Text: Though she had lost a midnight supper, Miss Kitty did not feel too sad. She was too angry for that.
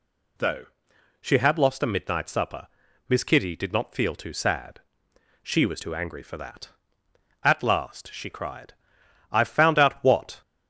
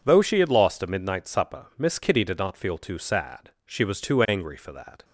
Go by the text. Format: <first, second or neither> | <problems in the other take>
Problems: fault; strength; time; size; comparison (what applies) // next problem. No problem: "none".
second | pauses between "Though" and "she"; noticeable; at 0.6 s; 0.54 s long // goes on to say "At last she cried I've found out what"; strong; from 7.4 s on; 2.9 s long